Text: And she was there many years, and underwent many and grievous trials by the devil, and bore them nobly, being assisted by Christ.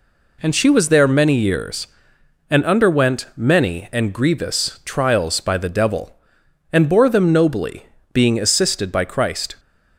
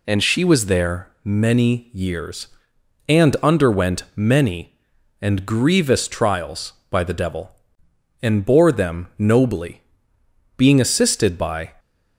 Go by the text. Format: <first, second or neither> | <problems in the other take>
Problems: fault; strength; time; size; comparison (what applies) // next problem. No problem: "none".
first | stops before "Christ"; at 11.7 s